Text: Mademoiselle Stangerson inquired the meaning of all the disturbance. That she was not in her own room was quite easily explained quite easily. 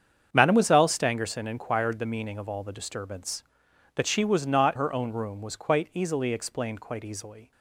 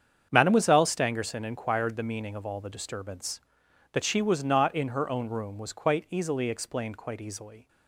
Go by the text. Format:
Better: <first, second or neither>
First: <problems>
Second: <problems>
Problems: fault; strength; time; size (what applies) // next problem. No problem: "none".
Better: second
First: starts louder than the rest; strong; until 1.3 s; 7.5 dB // skips "in"; at 4.7 s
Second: starts louder than the rest; strong; until 1.3 s; 7.5 dB